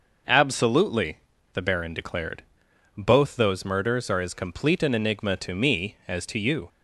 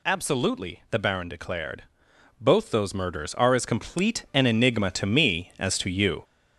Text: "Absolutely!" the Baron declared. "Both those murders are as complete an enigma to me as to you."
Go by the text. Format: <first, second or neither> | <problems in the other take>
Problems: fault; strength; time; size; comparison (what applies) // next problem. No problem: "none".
first | gets louder; noticeable; throughout; 4.5 dB